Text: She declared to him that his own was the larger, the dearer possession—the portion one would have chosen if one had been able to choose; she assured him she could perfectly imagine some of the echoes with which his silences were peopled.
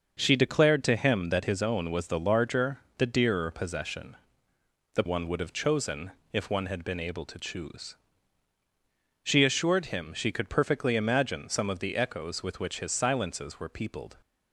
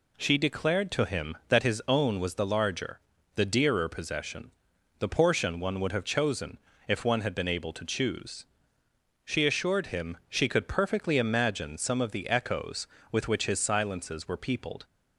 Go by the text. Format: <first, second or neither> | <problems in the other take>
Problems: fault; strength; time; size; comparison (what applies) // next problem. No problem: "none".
second | starts louder than the rest; noticeable; until 1.1 s; 6 dB // skips "portion"; at 5.0 s // pauses between "chosen" and "if"; slight; at 6.1 s; 0.20 s long; slight in the second